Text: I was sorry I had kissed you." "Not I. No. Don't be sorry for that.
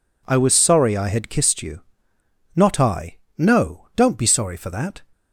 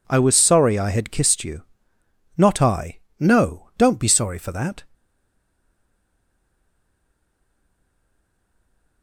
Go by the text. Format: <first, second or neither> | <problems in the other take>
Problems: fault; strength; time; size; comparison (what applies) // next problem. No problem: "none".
first | stays silent after the last word; strong; from 4.9 s on; 4.1 s long